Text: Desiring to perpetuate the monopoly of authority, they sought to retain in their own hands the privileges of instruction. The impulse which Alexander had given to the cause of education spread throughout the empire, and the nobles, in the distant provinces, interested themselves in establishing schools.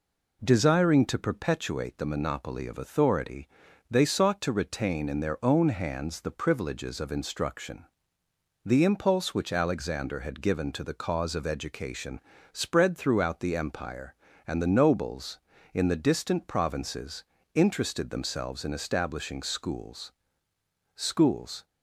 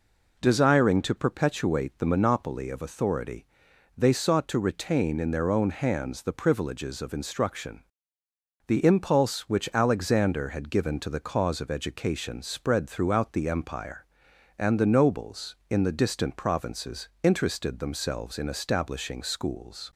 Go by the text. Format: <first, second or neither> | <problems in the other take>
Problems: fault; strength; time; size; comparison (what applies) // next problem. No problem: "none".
second | pauses between "education" and "spread"; slight; at 12.2 s; 0.34 s long // says "schools" twice; at 20.9 s